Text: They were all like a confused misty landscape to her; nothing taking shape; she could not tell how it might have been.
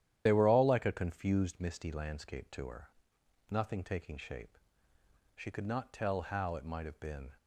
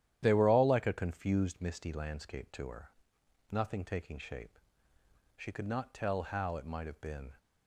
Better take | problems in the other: second | loses the start of "They"; at 0.2 s; 35 ms // starts louder than the rest; strong; until 1.2 s; 11 dB; strong in the second

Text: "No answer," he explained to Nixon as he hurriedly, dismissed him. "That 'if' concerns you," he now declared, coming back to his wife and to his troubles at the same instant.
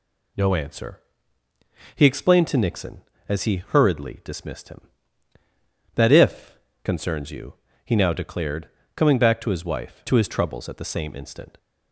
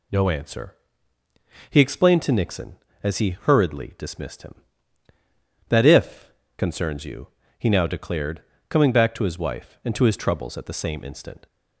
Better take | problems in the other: second | pauses between "if" and "concerns"; slight; at 6.5 s; 0.26 s long; slight in the second // skips "and"; at 10.0 s

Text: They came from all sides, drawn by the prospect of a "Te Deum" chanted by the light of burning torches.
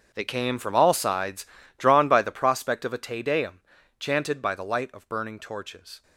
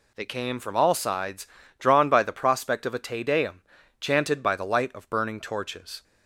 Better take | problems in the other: second | gets quieter; strong; throughout; 15.5 dB // pauses between "Deum" and "chanted"; at 3.6 s; 0.38 s long; also in the second

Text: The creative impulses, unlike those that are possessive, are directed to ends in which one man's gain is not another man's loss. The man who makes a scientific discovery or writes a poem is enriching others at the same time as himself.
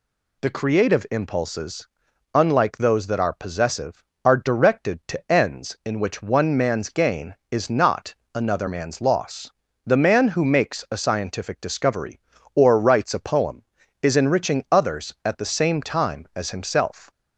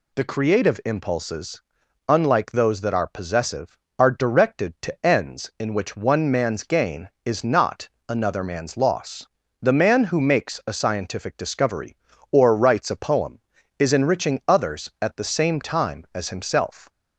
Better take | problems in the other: neither | pauses between "not" and "another"; slight; the same in both

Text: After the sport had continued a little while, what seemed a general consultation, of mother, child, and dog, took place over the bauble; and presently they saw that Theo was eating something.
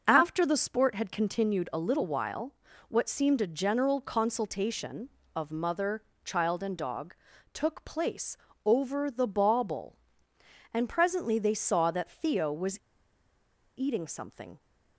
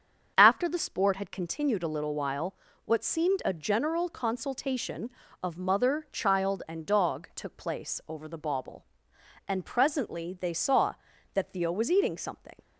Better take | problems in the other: second | starts louder than the rest; noticeable; until 1.0 s; 6 dB; also in the second // pauses between "place" and "over"; slight; at 8.3 s; 0.30 s long // pauses between "was" and "eating"; at 12.7 s; 1.0 s long

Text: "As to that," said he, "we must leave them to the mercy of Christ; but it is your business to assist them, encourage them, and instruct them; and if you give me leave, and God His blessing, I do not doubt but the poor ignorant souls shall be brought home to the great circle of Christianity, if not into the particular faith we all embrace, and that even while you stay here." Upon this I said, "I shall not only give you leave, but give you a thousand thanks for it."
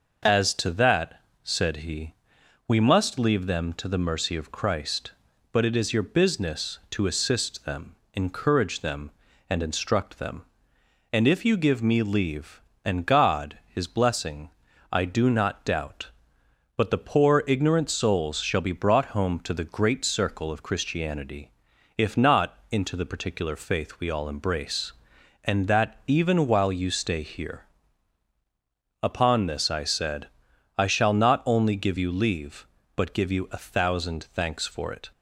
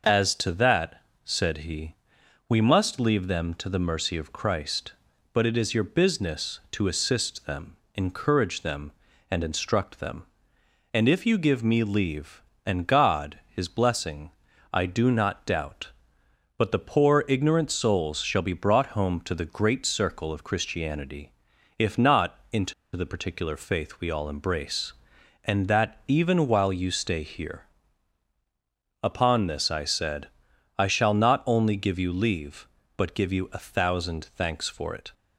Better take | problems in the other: first | pauses between "into" and "the"; slight; at 22.7 s; 0.22 s long

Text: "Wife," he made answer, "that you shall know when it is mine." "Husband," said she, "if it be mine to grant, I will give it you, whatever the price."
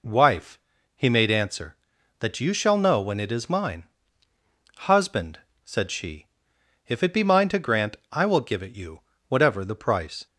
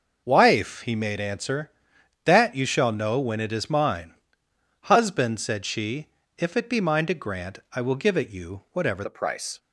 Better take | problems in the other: first | changes voice at "the"; from 9.0 s on; 0.5 s long

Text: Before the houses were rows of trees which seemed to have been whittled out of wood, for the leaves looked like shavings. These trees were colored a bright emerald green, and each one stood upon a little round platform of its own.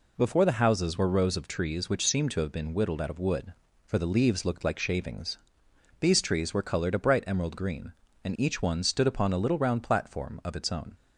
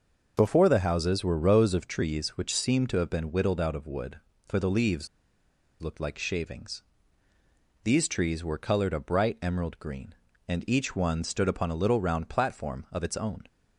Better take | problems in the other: first | pauses between "leaves" and "looked"; noticeable; at 5.0 s; 0.75 s long

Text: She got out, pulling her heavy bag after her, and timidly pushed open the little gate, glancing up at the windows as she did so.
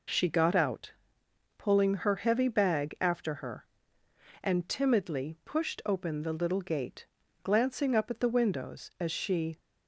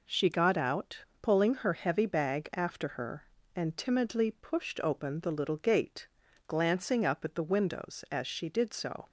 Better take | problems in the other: second | stops before "did so"; at 9.5 s

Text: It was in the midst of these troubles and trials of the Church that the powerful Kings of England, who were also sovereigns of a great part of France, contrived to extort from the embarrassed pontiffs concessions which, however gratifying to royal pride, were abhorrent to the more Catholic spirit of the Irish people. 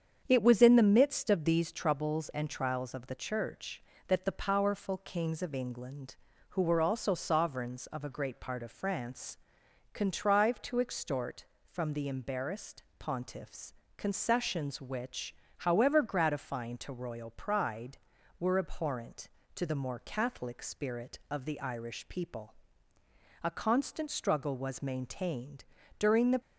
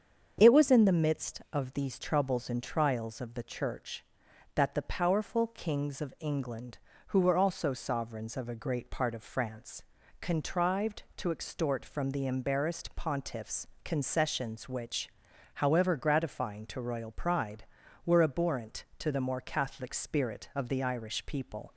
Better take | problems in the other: second | starts louder than the rest; strong; until 1.2 s; 7.5 dB; strong in the second // pauses between "embarrassed" and "pontiffs"; slight; at 12.8 s; 0.16 s long // pauses between "pontiffs" and "concessions"; slight; at 13.7 s; 0.22 s long; slight in the second // goes on to say "A constant struggle was maintained during the"; strong; from 23.4 s on; 2.9 s long

